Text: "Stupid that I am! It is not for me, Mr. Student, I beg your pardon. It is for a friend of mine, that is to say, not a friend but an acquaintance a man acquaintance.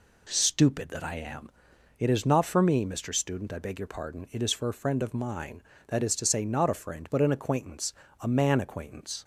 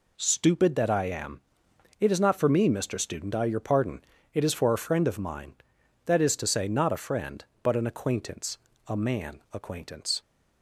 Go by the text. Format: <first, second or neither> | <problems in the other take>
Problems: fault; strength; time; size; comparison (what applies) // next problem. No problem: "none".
first | skips "beg"; at 3.4 s // pauses between "acquaintance" and "a"; slight; at 8.5 s; 0.30 s long; slight in the first